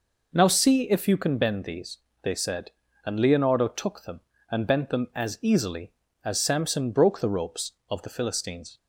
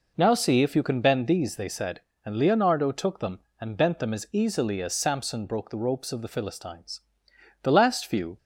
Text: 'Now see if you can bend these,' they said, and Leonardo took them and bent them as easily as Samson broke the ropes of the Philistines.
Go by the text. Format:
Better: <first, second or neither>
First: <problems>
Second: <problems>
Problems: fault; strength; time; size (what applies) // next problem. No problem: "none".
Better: first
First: none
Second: goes on to say "The last few"; noticeable; from 7.6 s on; 0.74 s long